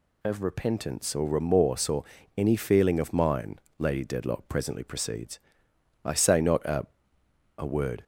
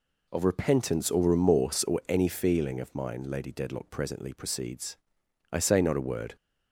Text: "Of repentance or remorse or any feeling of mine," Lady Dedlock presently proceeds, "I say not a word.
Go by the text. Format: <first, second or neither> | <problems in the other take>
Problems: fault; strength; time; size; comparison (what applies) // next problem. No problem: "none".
second | pauses between "or" and "any"; slight; at 2.0 s; 0.34 s long // says "a" twice; at 7.5 s